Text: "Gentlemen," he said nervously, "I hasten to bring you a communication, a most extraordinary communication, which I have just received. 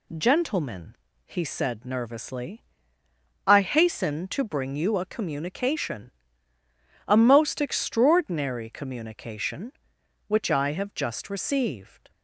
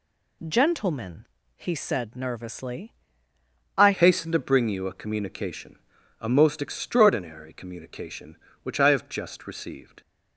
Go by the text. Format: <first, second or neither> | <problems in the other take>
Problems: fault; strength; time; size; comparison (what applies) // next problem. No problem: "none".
first | changes voice at "hasten"; from 3.9 s on; 6.1 s long